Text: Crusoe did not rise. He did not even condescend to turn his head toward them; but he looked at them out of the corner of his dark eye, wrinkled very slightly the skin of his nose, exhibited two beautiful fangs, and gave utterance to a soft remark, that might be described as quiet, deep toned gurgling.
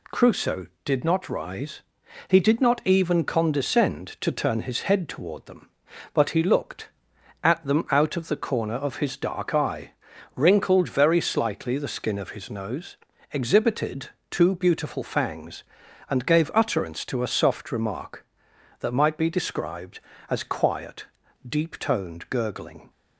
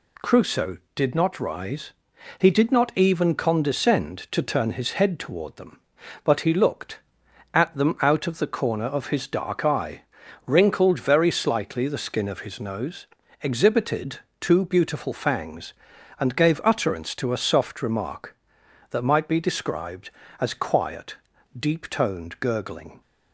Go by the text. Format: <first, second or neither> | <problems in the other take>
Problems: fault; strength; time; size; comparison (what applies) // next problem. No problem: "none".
neither | pauses between "exhibited" and "two"; slight; the same in both